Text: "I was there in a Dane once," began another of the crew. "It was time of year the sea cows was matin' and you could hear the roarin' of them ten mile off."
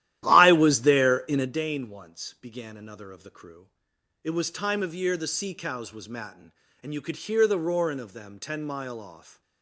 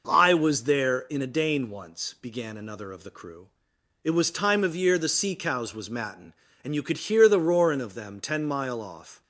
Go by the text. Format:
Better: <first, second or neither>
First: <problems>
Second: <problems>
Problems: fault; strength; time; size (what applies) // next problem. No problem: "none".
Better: second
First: starts louder than the rest; strong; until 1.6 s; 13 dB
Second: none